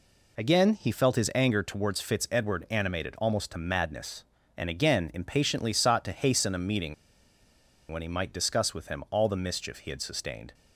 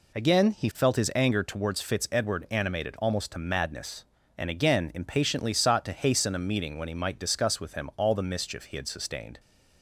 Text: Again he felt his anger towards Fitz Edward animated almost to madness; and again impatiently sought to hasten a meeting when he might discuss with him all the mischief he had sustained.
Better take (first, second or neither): second